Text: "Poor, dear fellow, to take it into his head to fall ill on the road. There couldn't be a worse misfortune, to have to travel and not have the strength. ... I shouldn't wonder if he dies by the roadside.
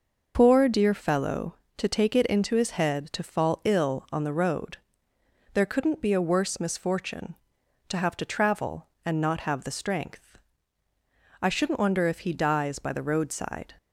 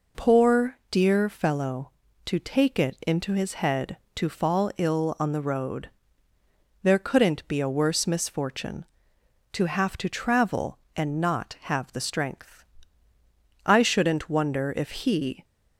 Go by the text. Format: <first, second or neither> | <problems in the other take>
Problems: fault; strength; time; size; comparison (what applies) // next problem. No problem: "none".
first | stops before "dies by the roadside"; at 15.4 s